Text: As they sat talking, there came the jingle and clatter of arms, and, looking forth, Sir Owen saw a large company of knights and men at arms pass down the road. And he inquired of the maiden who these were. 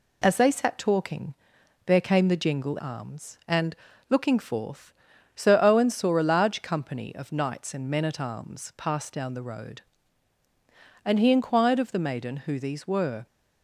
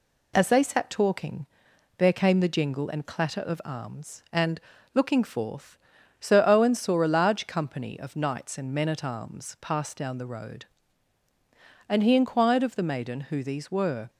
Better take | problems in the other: second | skips "and clatter of"; at 2.7 s

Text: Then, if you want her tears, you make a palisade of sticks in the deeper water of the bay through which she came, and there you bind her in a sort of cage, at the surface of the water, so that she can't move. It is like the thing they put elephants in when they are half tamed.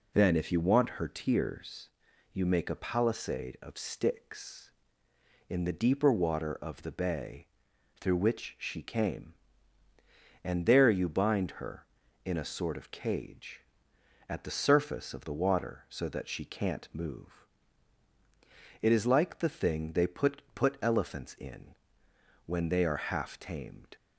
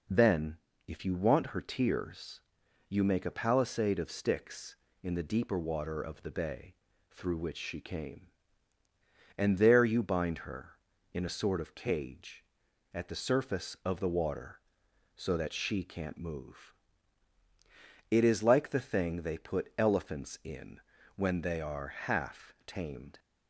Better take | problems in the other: second | pauses between "bay" and "through"; noticeable; at 7.4 s; 0.54 s long; slight in the second // says "put" twice; at 20.5 s // pauses between "in" and "when"; noticeable; at 21.7 s; 0.72 s long; also in the second

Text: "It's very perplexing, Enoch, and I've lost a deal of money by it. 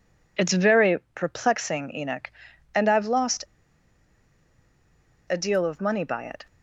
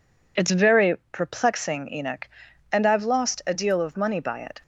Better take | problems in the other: second | pauses between "very" and "perplexing"; slight; at 0.9 s; 0.18 s long; slight in the second // pauses between "lost" and "a"; strong; at 3.4 s; 1.8 s long

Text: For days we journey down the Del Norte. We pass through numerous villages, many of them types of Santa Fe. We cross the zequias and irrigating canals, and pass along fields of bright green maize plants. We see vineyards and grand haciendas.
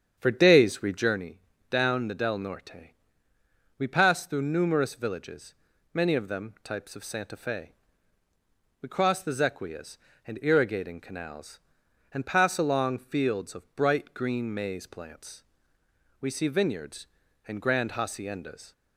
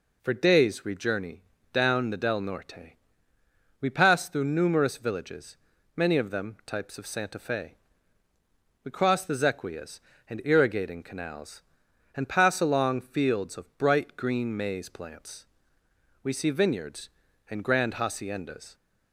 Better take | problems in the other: second | starts louder than the rest; strong; until 1.3 s; 8 dB // pauses between "journey" and "down"; slight; at 1.3 s; 0.32 s long; slight in the second

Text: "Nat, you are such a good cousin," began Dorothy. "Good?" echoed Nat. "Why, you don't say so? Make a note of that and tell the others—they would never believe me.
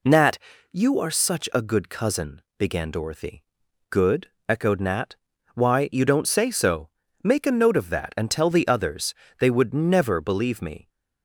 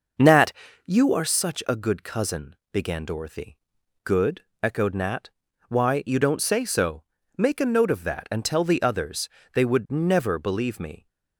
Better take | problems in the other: first | starts louder than the rest; noticeable; until 1.4 s; 6 dB

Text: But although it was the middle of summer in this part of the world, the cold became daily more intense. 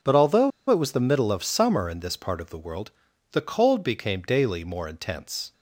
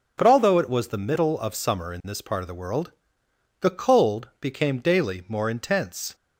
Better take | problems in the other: second | pauses between "although" and "it"; slight; at 0.5 s; 0.20 s long

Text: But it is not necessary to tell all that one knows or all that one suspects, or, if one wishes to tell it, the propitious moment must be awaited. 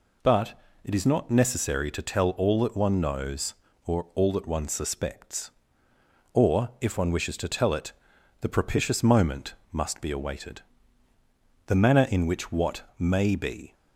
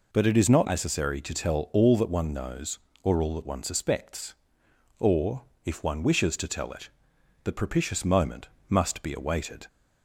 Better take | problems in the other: second | pauses between "But" and "it"; slight; at 0.5 s; 0.30 s long // pauses between "moment" and "must"; slight; at 9.5 s; 0.18 s long; slight in the second // goes on to say "The manner in which what may be"; strong; from 11.6 s on; 2.0 s long

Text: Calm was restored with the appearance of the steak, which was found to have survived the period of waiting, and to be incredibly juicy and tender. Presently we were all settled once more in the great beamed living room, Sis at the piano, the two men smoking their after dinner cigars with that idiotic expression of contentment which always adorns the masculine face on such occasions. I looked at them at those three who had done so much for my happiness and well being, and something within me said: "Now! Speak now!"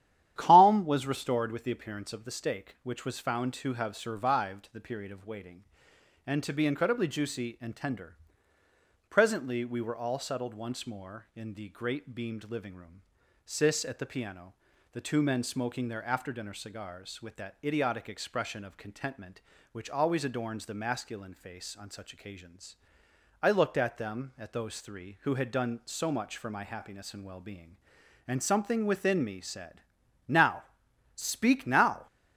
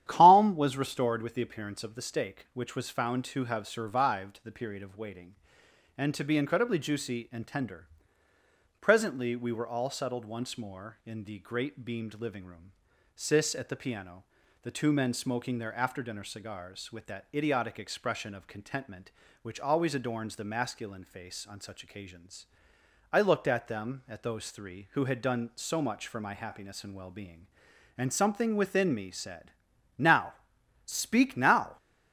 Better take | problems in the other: neither | starts louder than the rest; strong; the same in both

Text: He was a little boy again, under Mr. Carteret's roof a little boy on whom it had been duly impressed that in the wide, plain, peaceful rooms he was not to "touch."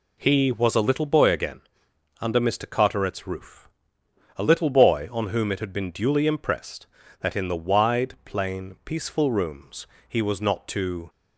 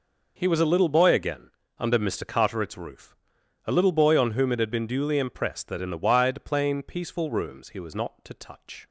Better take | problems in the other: second | pauses between "roof" and "a"; noticeable; at 3.6 s; 0.74 s long; noticeable in the second // pauses between "rooms" and "he"; slight; at 9.8 s; 0.20 s long // stops before "touch"; at 11.0 s

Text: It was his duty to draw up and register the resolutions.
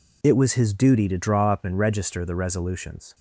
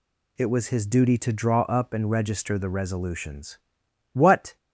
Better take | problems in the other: first | goes on to say "What"; slight; from 4.1 s on; 0.44 s long

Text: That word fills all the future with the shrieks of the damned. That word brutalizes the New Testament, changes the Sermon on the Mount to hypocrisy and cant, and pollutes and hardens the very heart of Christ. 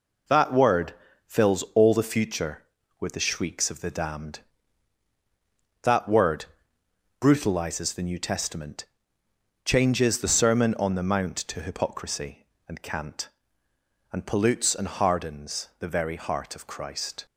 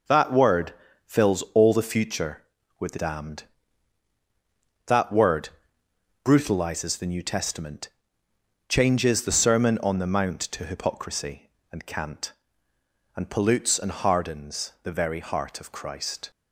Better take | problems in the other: first | pauses between "word" and "fills"; slight; at 0.7 s; 0.34 s long; slight in the first // skips "shrieks of the"; at 2.9 s // pauses between "word" and "brutalizes"; noticeable; at 5.5 s; 0.74 s long; noticeable in the first

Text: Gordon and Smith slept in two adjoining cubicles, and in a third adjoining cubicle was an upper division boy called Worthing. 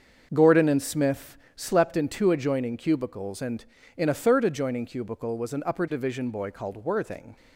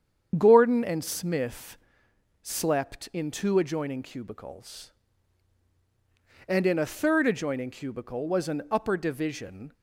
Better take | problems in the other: first | starts louder than the rest; strong; until 1.3 s; 7.5 dB; also in the first // pauses between "Smith" and "slept"; noticeable; at 1.7 s; 0.66 s long; slight in the first // stops before "boy called Worthing"; at 9.7 s

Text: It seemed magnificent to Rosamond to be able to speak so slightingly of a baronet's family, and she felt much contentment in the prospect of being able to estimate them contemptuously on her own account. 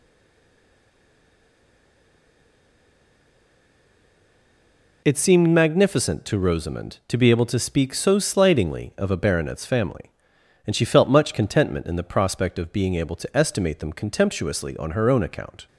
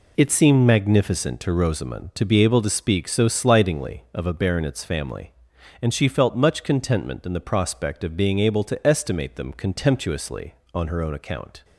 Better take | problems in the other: second | stays silent before the first word; strong; until 5.0 s; 5.0 s long

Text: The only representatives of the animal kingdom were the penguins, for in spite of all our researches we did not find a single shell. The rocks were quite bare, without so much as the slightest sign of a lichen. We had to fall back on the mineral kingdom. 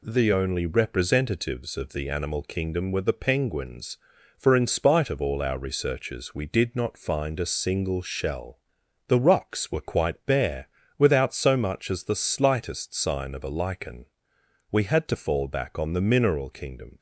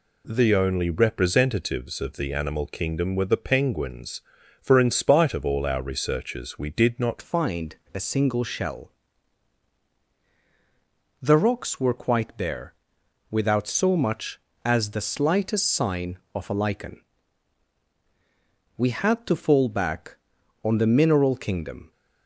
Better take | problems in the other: first | changes voice at "find"; from 7.2 s on; 14.7 s long // pauses between "find" and "a"; slight; at 7.7 s; 0.18 s long

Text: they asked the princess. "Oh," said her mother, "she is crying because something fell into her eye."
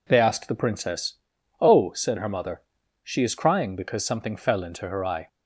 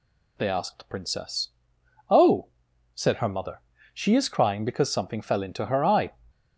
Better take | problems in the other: neither | none

